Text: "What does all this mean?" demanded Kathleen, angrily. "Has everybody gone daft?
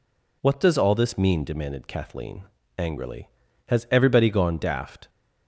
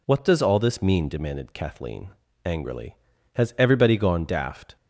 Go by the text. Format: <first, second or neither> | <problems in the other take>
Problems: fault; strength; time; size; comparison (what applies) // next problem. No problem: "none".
neither | none